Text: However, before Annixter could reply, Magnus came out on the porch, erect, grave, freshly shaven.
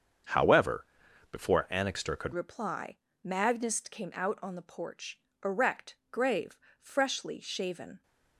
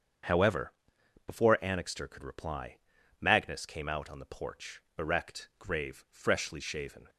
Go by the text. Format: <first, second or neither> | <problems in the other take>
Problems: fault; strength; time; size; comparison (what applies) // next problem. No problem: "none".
second | starts louder than the rest; until 1.7 s; 7 dB; strong in the second // changes voice at "reply"; from 2.3 s on; 5.7 s long